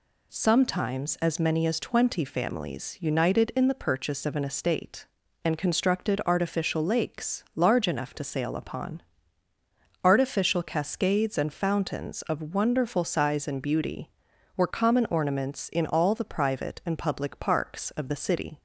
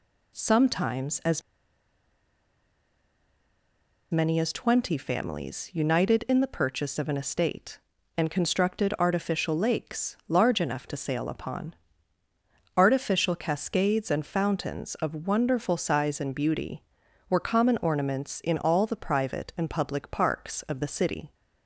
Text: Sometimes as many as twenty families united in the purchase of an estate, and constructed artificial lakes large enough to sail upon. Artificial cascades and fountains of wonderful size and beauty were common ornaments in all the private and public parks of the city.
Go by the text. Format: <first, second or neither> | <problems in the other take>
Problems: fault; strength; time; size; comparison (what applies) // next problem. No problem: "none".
first | pauses between "as" and "many"; strong; at 1.4 s; 2.7 s long